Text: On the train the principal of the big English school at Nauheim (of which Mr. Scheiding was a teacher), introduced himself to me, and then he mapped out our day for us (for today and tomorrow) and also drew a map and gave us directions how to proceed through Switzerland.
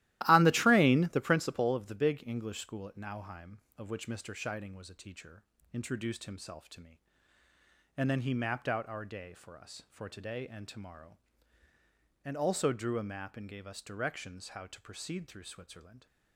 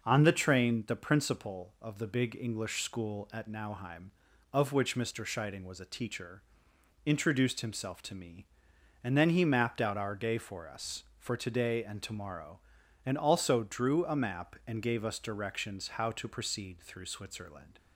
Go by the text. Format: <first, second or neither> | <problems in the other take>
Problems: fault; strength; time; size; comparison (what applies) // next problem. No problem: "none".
second | starts louder than the rest; strong; until 1.4 s; 15.5 dB